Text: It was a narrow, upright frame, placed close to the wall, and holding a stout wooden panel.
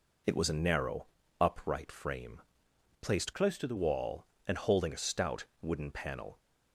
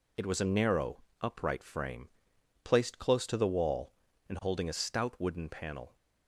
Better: second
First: changes voice from "close" to "the"; from 3.3 to 3.7 s; 0.4 s long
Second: none

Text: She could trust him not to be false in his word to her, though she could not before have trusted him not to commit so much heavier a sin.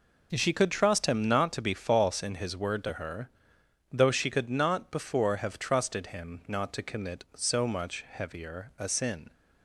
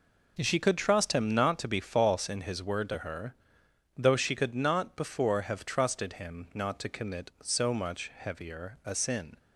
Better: neither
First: none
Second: none

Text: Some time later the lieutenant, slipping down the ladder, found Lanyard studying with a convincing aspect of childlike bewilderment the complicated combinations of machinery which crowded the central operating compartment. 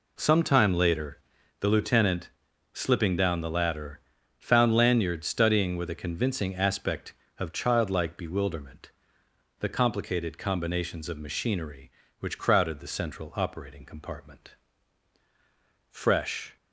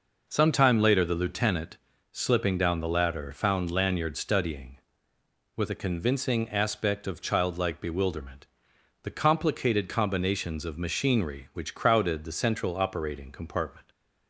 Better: second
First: pauses between "later" and "the"; at 1.1 s; 0.42 s long // pauses between "bewilderment" and "the"; noticeable; at 8.9 s; 0.68 s long // goes on to say "Fresh"; noticeable; from 15.9 s on; 0.66 s long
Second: pauses between "bewilderment" and "the"; noticeable; at 8.4 s; 0.58 s long

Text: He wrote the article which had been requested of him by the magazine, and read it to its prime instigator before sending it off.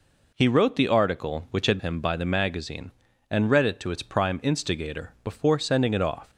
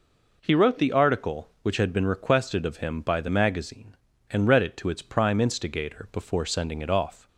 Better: second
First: skips "been requested of"; at 1.7 s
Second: none

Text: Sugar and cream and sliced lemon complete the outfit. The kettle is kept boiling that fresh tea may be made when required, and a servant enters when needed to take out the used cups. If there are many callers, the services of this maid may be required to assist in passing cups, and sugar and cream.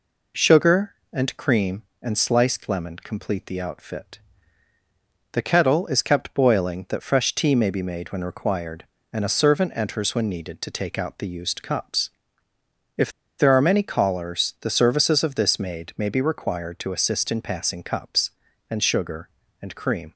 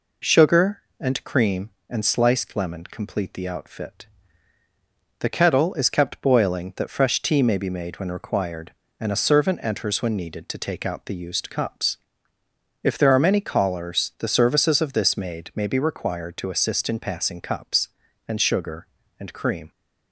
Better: second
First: pauses between "If" and "there"; slight; at 13.1 s; 0.28 s long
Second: none

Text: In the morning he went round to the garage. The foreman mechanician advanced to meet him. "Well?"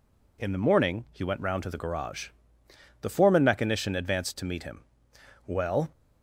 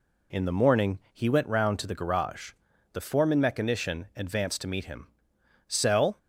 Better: first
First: none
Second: says "Cell" for "Well"; at 5.6 s

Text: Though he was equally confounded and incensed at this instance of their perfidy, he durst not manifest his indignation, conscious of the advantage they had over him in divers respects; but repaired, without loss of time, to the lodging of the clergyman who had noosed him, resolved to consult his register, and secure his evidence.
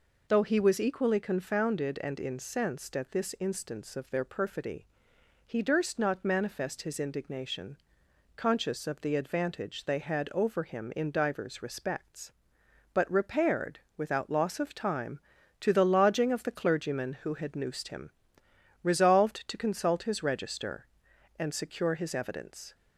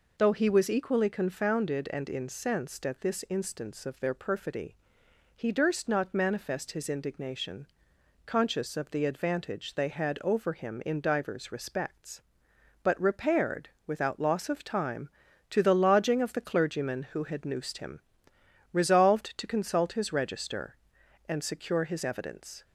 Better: neither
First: none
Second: none

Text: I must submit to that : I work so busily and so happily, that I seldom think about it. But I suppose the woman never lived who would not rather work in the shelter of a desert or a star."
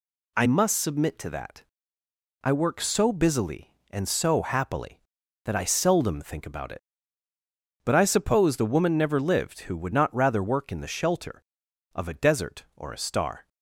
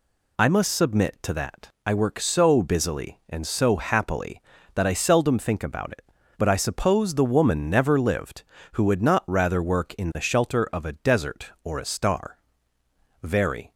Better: first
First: none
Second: goes on to say "Very"; from 13.2 s on; 0.52 s long

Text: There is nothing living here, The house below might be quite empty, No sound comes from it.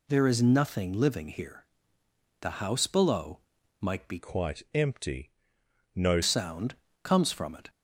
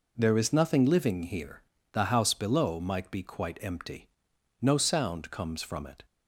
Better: second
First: pauses between "below" and "might"; at 3.3 s; 0.42 s long // changes voice from "quite" to "No"; from 4.1 to 6.2 s; 2.1 s long // pauses between "sound" and "comes"; slight; at 6.7 s; 0.30 s long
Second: none

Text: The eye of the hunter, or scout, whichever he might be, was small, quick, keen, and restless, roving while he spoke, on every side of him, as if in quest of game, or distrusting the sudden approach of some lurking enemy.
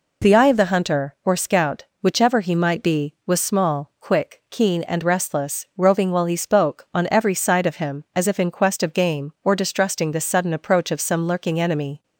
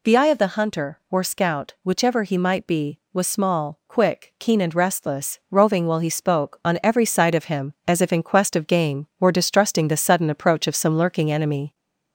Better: first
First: none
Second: gets louder; slight; throughout; 2.5 dB

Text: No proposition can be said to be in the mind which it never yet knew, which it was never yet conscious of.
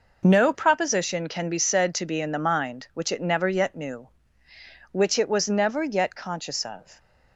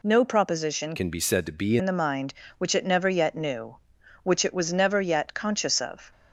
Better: first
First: none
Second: changes voice from "can" to "be"; from 0.9 to 1.7 s; 0.8 s long

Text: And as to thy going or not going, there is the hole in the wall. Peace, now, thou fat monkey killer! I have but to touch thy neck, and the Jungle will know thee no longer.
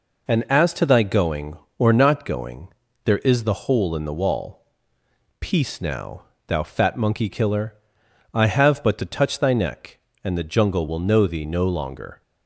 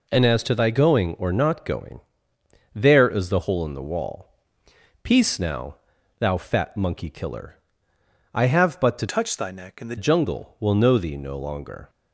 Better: first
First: none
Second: changes voice from "touch" to "the"; from 9.0 to 9.9 s; 0.9 s long

